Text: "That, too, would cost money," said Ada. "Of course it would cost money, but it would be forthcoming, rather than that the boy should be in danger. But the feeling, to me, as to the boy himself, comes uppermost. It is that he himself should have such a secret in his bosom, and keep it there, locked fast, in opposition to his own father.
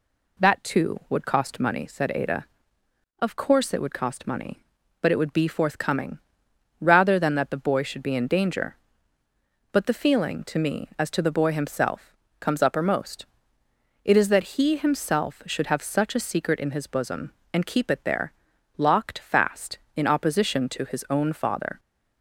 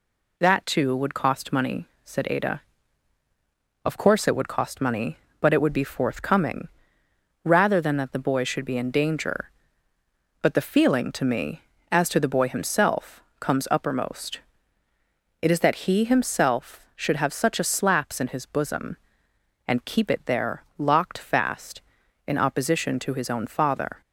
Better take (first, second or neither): first